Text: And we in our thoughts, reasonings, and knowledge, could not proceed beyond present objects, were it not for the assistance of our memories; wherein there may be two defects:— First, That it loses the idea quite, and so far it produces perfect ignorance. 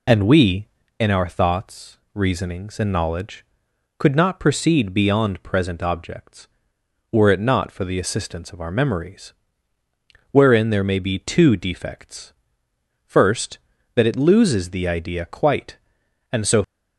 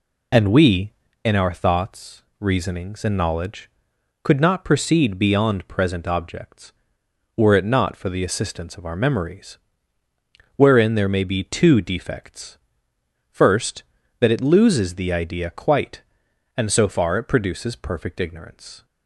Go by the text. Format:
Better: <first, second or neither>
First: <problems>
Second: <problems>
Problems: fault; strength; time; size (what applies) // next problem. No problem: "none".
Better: second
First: stops before "far it produces perfect ignorance"; at 16.6 s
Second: none